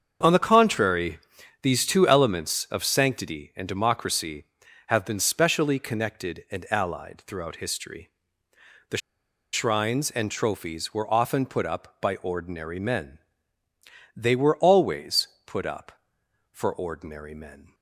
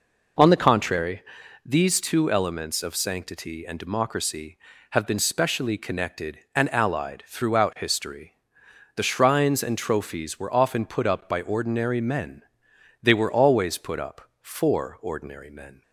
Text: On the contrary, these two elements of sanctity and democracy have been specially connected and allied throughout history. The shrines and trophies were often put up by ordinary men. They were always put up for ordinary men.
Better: second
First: starts louder than the rest; strong; until 1.6 s; 7 dB // pauses between "The" and "shrines"; noticeable; at 9.0 s; 0.54 s long // pauses between "always" and "put"; slight; at 15.2 s; 0.18 s long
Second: none

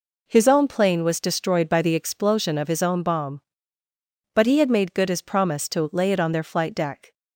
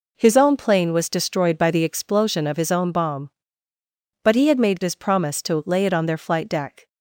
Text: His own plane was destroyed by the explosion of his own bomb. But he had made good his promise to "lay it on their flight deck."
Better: first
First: none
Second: skips "good"; at 4.8 s

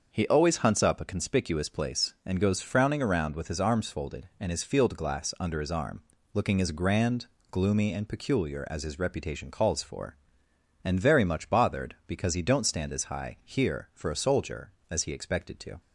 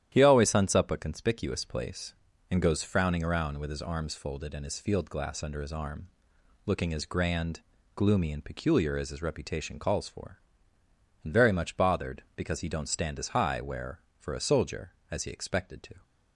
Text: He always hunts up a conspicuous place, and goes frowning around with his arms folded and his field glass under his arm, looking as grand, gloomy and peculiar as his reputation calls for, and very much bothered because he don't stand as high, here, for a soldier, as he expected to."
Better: first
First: starts louder than the rest; until 1.1 s; 6.5 dB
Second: starts louder than the rest; strong; until 1.1 s; 11 dB // says "where" for "here"; at 13.5 s

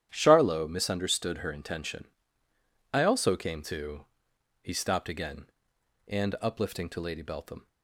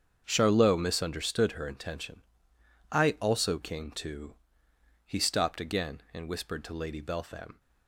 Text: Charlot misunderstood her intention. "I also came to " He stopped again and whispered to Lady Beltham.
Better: second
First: starts louder than the rest; strong; until 1.1 s; 11 dB // says "uplifting" for "whispered"; at 6.4 s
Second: starts louder than the rest; strong; until 1.2 s; 7.5 dB

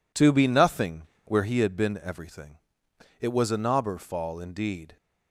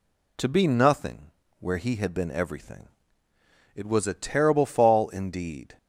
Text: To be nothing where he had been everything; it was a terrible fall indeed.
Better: second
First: pauses between "nothing" and "where"; slight; at 1.0 s; 0.22 s long // says "knobber" for "terrible"; at 3.5 s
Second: pauses between "nothing" and "where"; slight; at 1.3 s; 0.28 s long

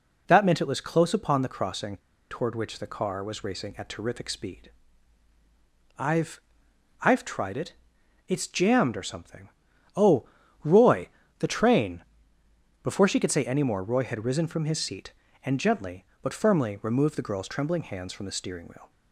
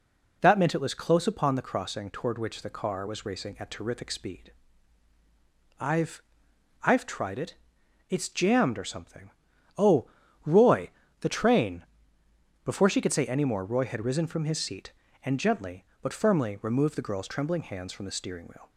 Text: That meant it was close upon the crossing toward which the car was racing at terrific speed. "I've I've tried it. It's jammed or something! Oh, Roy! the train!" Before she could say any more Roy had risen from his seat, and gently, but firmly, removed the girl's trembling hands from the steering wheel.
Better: second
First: pauses between "crossing" and "toward"; slight; at 1.9 s; 0.33 s long // pauses between "I've" and "I've"; noticeable; at 6.3 s; 0.62 s long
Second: pauses between "I've" and "I've"; noticeable; at 6.2 s; 0.62 s long

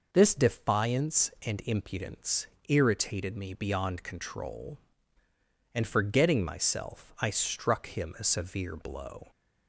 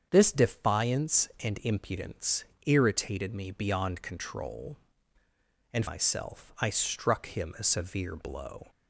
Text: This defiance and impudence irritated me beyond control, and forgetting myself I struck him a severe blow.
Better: first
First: pauses between "impudence" and "irritated"; slight; at 2.4 s; 0.22 s long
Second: starts louder than the rest; strong; until 1.1 s; 7.5 dB // pauses between "impudence" and "irritated"; slight; at 2.4 s; 0.22 s long // skips "forgetting"; at 5.8 s

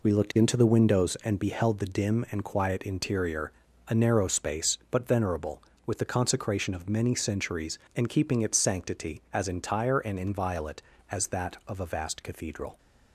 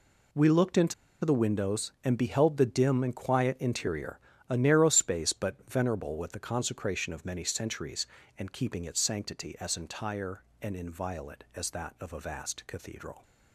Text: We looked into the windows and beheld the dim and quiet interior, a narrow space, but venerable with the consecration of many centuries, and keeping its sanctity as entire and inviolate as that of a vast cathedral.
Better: first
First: none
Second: pauses between "into" and "the"; slight; at 0.9 s; 0.30 s long

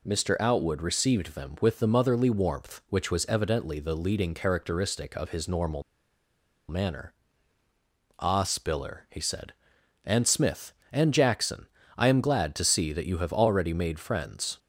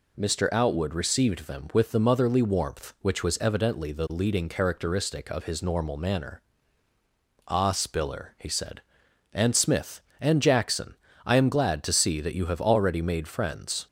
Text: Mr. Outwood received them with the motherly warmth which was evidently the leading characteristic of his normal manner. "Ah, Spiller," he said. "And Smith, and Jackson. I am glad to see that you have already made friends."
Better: second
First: pauses between "normal" and "manner"; noticeable; at 5.8 s; 0.86 s long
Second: none

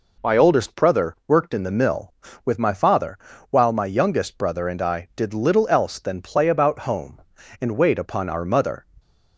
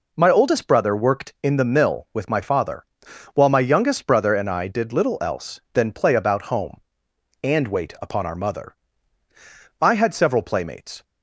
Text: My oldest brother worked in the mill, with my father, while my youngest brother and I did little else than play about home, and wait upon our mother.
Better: first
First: none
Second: goes on to say "I had several playmates"; noticeable; from 9.8 s on; 1.2 s long

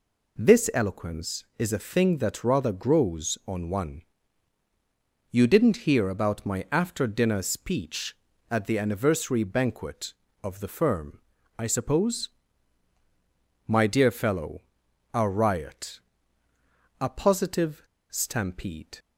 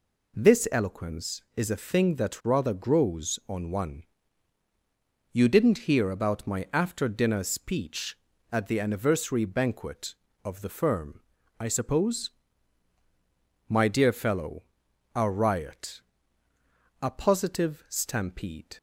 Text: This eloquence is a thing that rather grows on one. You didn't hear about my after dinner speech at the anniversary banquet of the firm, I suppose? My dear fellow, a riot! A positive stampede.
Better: second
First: pauses between "positive" and "stampede"; slight; at 17.8 s; 0.28 s long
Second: none

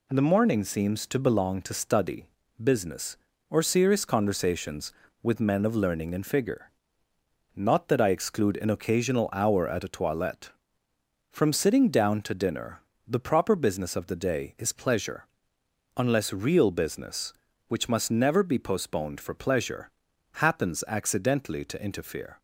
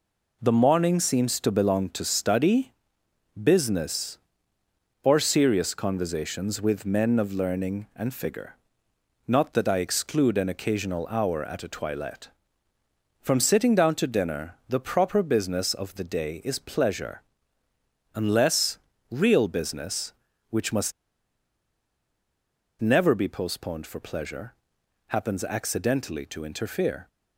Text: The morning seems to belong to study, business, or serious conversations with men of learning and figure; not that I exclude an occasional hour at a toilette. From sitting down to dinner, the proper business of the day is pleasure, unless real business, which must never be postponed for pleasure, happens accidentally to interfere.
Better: first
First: none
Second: pauses between "unless" and "real"; slight; at 18.7 s; 0.32 s long // pauses between "must" and "never"; strong; at 20.9 s; 1.8 s long

